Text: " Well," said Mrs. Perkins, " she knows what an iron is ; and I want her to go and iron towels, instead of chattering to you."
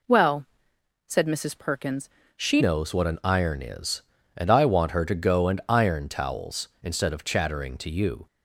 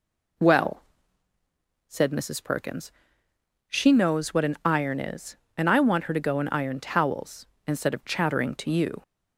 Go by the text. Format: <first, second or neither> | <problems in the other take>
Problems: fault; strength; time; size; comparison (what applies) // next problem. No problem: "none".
second | changes voice at "knows"; from 2.5 s on; 5.7 s long